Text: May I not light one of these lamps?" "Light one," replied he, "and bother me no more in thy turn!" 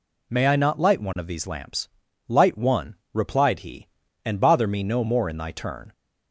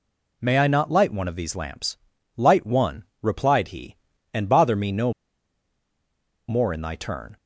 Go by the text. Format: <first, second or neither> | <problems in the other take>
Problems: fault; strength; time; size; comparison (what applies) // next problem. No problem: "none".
first | pauses between "no" and "more"; strong; at 5.1 s; 1.3 s long